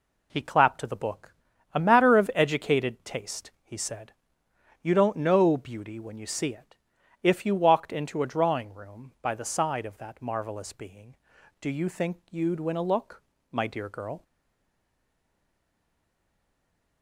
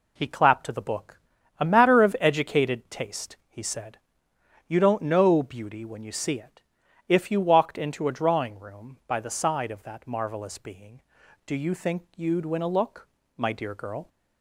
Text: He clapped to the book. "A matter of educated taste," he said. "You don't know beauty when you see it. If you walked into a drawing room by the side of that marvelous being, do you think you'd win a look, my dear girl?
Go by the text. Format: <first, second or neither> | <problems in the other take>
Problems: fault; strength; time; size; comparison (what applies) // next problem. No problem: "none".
second | stays silent after the last word; strong; from 14.2 s on; 2.8 s long